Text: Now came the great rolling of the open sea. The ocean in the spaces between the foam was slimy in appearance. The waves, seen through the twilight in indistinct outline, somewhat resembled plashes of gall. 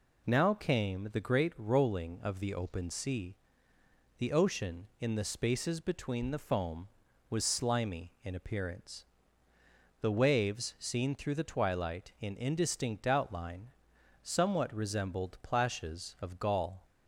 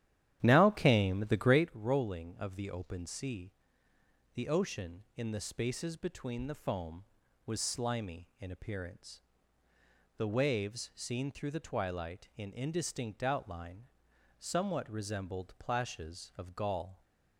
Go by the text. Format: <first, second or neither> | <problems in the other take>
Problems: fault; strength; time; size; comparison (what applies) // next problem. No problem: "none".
first | starts louder than the rest; strong; until 1.8 s; 11 dB